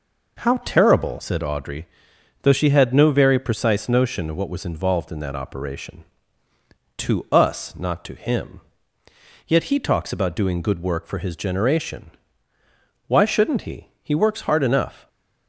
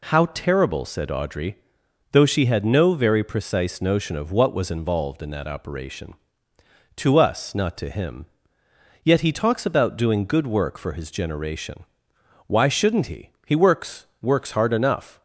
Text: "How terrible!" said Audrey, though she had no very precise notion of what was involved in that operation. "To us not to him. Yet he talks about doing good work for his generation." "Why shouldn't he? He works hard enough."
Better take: first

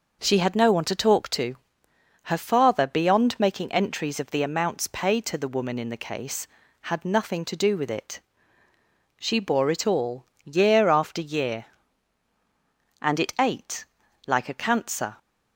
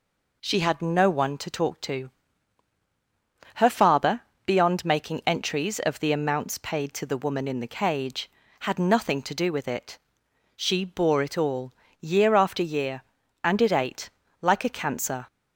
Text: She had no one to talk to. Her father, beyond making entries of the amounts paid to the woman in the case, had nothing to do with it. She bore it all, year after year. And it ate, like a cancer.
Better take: first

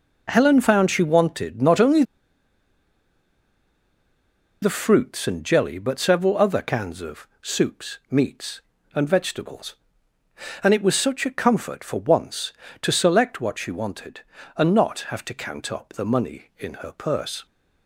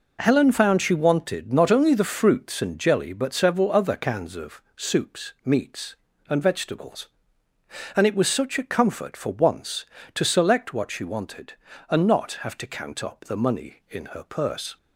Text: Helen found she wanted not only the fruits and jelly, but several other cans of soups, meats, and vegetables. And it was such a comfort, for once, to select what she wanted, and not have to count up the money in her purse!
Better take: second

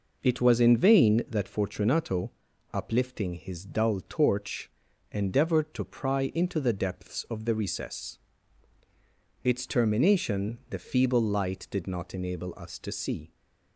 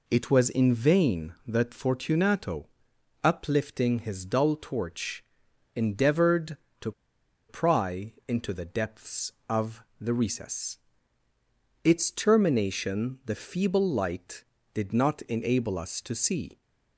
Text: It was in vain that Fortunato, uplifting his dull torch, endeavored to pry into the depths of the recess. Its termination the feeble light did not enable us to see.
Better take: first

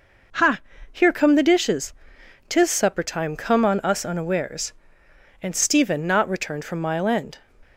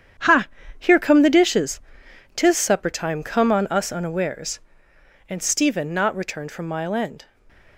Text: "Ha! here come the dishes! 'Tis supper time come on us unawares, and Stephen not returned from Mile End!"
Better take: first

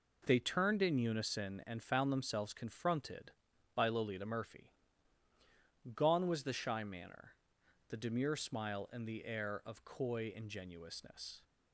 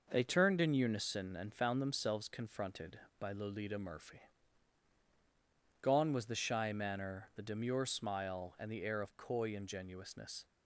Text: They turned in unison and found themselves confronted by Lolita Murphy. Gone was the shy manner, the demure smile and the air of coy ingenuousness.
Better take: neither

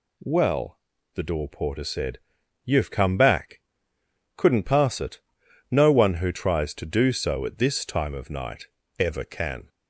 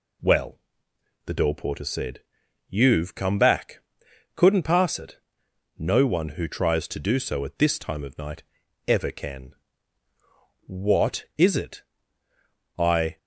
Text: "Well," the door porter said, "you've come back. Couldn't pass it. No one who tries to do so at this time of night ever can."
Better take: first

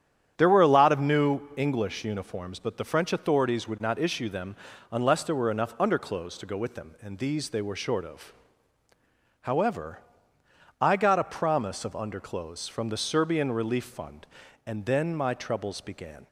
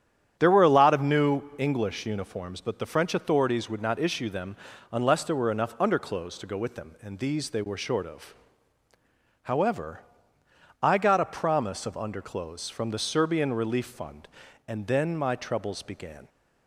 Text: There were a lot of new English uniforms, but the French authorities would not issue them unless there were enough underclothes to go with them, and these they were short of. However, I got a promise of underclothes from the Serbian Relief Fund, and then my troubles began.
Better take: neither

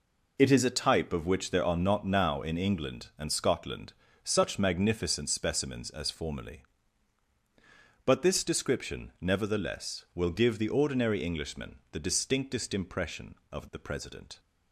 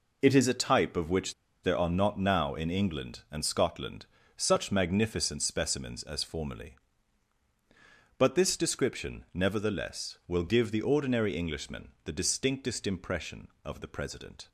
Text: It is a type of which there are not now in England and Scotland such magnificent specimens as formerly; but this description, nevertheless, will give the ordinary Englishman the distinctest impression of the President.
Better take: first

